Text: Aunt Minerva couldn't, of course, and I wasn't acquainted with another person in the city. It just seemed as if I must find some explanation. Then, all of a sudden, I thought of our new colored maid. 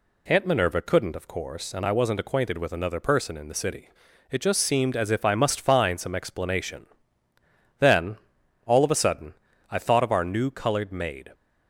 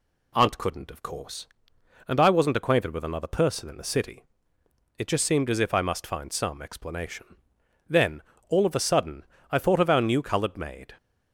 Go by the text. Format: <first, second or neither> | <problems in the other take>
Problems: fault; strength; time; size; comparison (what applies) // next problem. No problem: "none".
first | skips "Minerva"; at 0.5 s